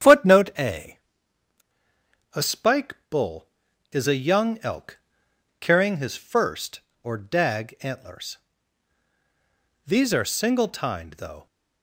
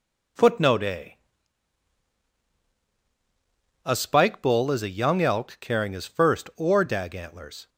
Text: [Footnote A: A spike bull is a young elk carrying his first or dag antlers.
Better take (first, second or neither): second